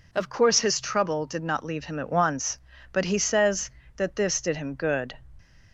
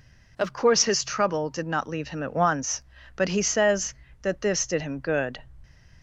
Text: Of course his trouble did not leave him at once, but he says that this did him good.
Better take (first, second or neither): neither